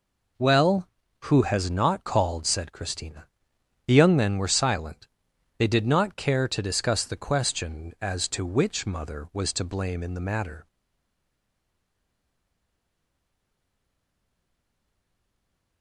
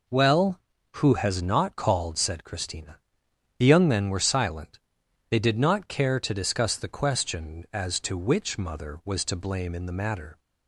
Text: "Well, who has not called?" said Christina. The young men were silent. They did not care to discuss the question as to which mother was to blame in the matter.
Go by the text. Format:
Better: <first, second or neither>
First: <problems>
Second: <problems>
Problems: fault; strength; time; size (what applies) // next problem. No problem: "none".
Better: second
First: stays silent after the last word; strong; from 10.6 s on; 5.2 s long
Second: none